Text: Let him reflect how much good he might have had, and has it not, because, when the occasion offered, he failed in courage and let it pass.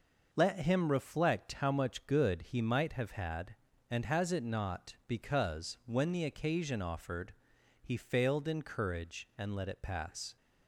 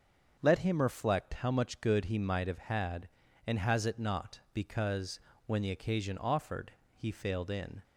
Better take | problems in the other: first | starts louder than the rest; until 1.4 s; 6.5 dB // stops before "courage and let it pass"; at 7.8 s

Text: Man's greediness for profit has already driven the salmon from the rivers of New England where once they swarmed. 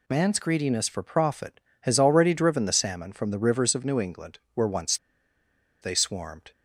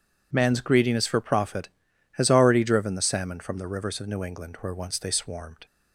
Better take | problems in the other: second | pauses between "England" and "where"; slight; at 4.3 s; 0.16 s long // pauses between "once" and "they"; noticeable; at 4.9 s; 0.85 s long

